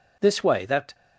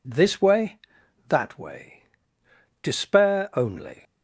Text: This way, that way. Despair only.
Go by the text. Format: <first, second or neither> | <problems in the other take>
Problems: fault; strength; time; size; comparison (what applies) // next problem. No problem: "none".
second | stops before "way Despair only"; at 0.9 s